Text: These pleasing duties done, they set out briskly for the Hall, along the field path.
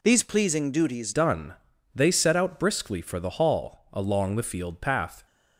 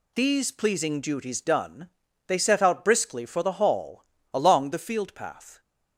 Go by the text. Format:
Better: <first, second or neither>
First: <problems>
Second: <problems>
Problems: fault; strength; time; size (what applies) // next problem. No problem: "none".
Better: second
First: changes voice at "done"; from 1.1 s on; 4.1 s long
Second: none